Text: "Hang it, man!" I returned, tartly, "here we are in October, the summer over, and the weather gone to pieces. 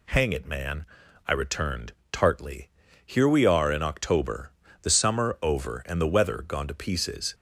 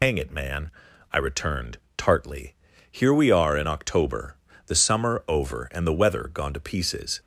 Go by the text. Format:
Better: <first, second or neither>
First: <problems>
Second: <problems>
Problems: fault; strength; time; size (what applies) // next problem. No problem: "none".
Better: first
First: none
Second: loses the start of "Hang"; at 0.0 s; 100 ms